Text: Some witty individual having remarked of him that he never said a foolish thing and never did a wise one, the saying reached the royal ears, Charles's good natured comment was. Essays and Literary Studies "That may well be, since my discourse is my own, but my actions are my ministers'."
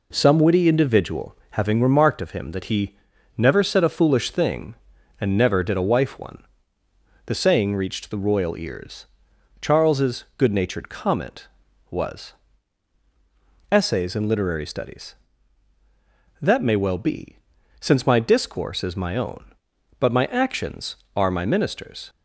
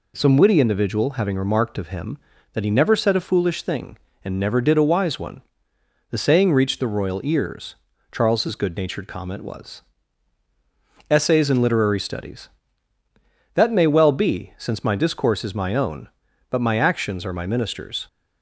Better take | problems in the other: second | pauses between "he" and "never"; at 2.9 s; 0.44 s long // says "wife" for "wise"; at 5.8 s

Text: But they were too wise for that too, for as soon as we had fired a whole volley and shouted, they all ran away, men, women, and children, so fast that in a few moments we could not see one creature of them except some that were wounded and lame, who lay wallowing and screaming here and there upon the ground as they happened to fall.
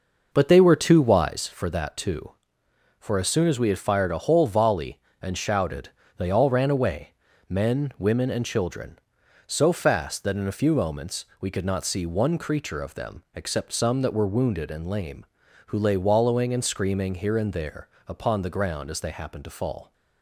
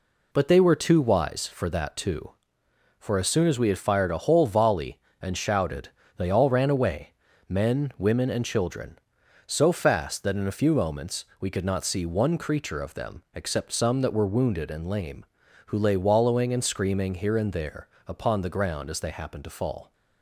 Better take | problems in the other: second | starts louder than the rest; noticeable; until 1.5 s; 5.5 dB // pauses between "there" and "upon"; slight; at 17.8 s; 0.18 s long; slight in the second

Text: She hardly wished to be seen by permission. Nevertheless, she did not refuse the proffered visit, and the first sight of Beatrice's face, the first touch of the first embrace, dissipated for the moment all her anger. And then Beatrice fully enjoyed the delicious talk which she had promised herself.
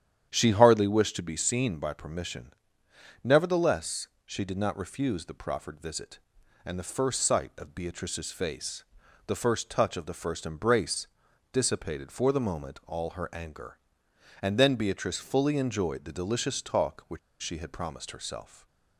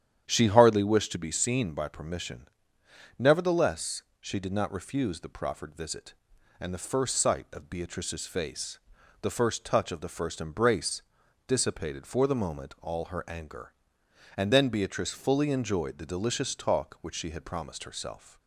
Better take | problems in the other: second | starts louder than the rest; strong; until 1.3 s; 9.5 dB; strong in the second // pauses between "which" and "she"; slight; at 17.1 s; 0.23 s long

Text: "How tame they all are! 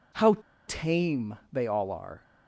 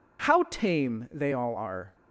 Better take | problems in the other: second | pauses between "How" and "tame"; slight; at 0.3 s; 0.32 s long

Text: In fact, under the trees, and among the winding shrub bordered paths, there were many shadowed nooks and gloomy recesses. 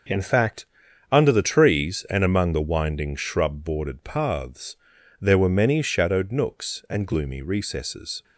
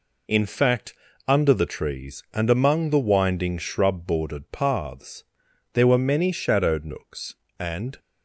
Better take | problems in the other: first | stops before "gloomy recesses"; at 7.9 s

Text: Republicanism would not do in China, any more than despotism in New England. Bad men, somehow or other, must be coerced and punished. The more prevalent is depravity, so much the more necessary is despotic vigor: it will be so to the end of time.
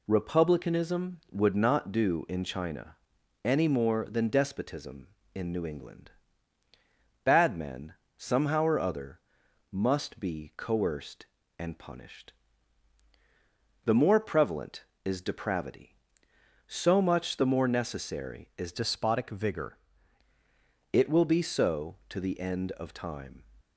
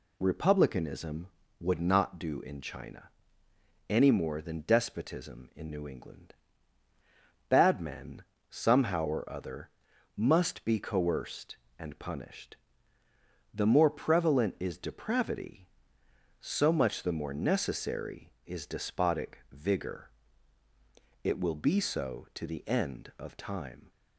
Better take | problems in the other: second | changes voice from "despotic" to "vigor"; from 18.7 to 19.7 s; 1.0 s long

